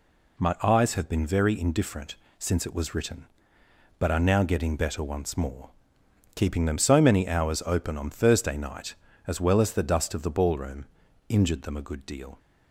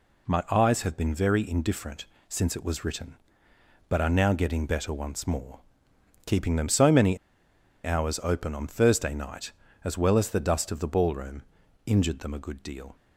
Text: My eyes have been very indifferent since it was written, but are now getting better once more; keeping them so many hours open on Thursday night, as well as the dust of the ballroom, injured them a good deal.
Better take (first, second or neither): first